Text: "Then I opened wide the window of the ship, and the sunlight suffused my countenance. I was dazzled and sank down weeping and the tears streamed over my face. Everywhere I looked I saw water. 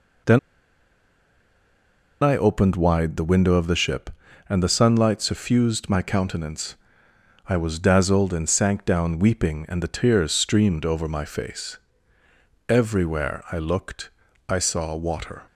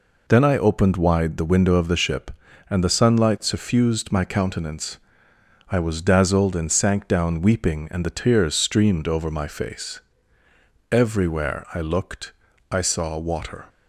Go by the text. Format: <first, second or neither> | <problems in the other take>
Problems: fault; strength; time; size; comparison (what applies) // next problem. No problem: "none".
second | pauses between "Then" and "I"; strong; at 0.3 s; 1.8 s long // pauses between "looked" and "I"; at 14.1 s; 0.38 s long; also in the second